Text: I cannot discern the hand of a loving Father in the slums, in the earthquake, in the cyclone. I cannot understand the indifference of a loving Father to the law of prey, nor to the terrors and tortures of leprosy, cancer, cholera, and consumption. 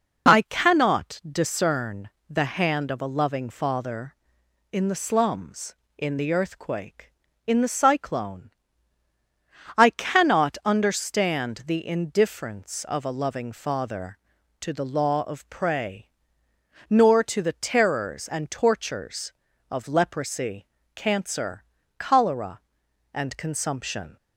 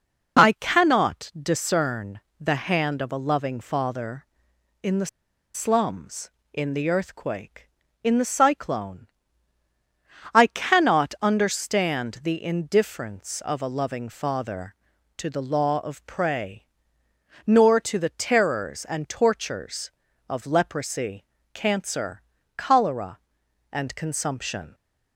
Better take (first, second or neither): first